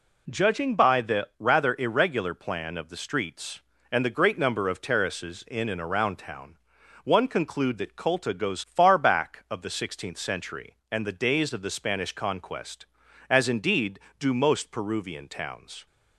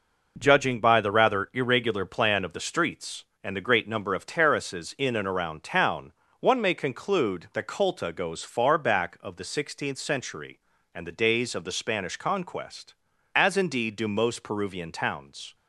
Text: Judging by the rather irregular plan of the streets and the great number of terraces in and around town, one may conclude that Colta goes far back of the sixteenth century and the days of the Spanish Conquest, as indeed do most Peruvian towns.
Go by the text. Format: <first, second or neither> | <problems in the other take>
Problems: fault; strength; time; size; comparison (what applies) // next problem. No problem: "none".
second | skips "may"; at 7.2 s